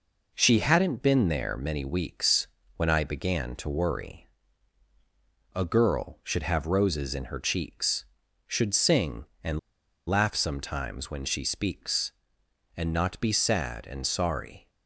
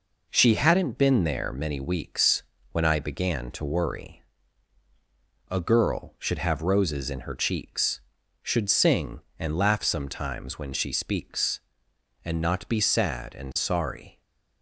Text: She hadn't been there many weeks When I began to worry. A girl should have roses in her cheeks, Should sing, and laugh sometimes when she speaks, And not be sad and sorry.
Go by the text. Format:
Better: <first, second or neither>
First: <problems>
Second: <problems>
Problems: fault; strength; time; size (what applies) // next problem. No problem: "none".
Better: second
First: pauses between "weeks" and "When"; slight; at 2.4 s; 0.28 s long // pauses between "and" and "laugh"; noticeable; at 9.5 s; 0.49 s long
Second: pauses between "weeks" and "When"; slight; at 2.4 s; 0.28 s long